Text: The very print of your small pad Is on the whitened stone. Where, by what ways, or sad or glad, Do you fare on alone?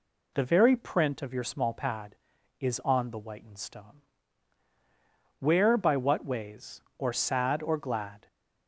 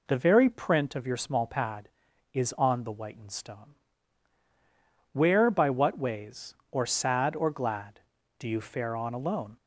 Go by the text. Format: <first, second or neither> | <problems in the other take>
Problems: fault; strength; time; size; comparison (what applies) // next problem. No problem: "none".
second | stops before "Do you fare on alone"; at 8.2 s